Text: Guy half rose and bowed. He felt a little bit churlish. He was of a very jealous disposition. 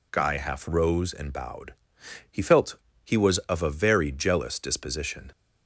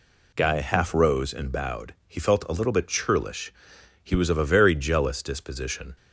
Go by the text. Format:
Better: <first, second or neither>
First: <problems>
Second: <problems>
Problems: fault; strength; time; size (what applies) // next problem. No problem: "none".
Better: second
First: skips "a little bit churlish"; at 2.9 s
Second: none